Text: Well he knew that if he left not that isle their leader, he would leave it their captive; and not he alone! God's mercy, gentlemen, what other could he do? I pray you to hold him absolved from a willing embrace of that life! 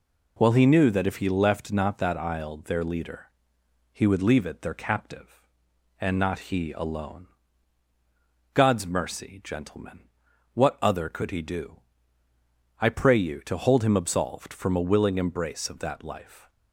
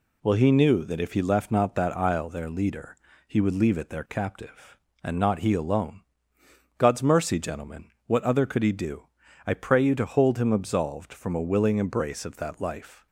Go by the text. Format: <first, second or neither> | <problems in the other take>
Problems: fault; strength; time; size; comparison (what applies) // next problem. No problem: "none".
neither | none